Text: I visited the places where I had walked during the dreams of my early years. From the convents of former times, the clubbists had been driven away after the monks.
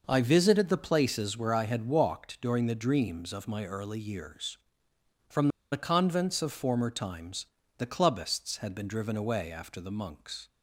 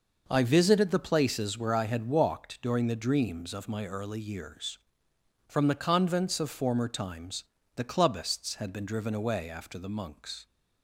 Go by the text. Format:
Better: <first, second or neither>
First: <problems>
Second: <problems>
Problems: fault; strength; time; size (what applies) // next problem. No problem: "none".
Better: second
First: pauses between "From" and "the"; slight; at 5.4 s; 0.22 s long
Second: none